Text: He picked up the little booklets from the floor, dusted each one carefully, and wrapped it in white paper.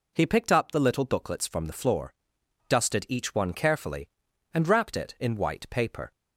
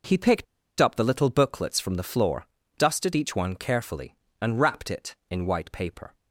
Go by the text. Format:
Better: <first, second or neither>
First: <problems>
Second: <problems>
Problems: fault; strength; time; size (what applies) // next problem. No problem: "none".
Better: first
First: none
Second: pauses between "picked" and "up"; slight; at 0.4 s; 0.35 s long